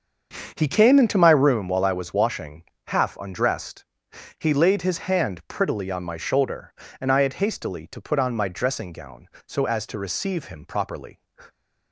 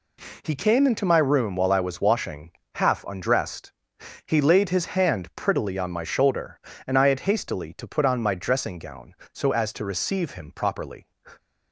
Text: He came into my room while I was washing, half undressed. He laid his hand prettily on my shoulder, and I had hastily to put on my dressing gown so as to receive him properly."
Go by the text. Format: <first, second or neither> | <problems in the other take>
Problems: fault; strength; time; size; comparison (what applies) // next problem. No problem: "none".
second | starts louder than the rest; until 1.7 s; 7 dB